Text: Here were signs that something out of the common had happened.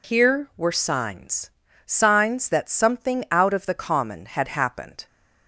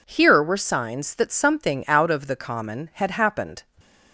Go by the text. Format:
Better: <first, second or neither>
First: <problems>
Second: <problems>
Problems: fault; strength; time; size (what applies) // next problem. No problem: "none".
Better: second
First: says "signs" twice; at 1.8 s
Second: none